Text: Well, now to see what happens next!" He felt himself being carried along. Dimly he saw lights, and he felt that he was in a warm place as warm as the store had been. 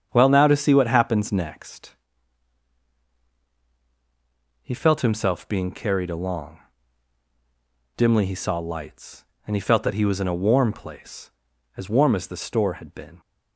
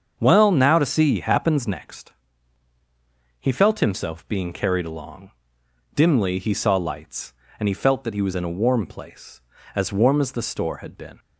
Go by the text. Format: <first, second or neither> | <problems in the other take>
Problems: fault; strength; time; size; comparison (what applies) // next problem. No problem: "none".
first | starts louder than the rest; until 1.1 s; 7 dB; strong in the first // skips "what"; at 1.2 s